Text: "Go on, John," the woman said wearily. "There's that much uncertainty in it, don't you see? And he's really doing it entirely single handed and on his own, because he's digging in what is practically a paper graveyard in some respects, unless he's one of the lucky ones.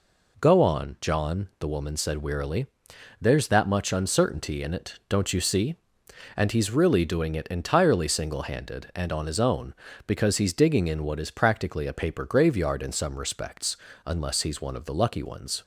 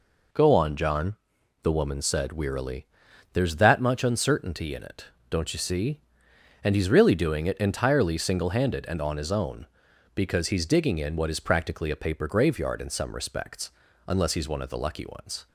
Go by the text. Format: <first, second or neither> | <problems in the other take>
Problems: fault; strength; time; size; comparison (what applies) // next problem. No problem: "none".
neither | none